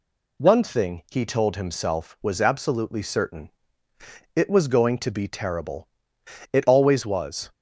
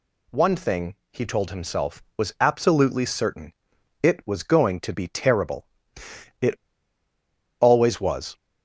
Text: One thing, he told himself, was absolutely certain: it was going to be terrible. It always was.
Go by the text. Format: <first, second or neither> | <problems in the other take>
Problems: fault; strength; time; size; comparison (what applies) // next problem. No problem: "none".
first | pauses between "It" and "always"; at 6.5 s; 1.0 s long